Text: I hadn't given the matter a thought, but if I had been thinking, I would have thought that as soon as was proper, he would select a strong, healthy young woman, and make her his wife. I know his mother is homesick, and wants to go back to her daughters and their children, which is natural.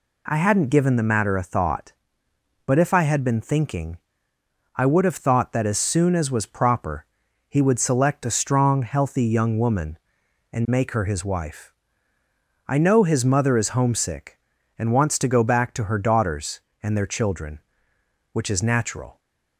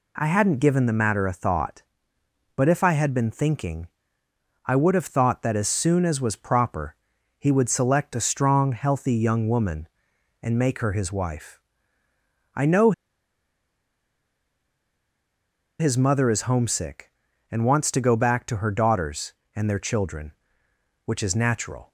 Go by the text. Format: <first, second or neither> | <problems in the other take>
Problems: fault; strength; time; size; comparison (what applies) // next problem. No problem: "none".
first | pauses between "know" and "his"; strong; at 12.9 s; 2.8 s long